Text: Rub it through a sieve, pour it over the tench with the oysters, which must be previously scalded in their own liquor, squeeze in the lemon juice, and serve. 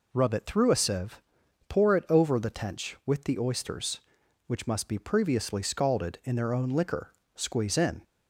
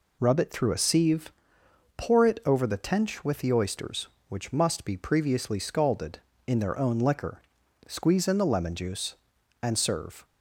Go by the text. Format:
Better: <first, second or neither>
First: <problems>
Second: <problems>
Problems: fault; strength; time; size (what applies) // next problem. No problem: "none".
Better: second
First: stops before "the lemon juice and serve"; at 8.0 s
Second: none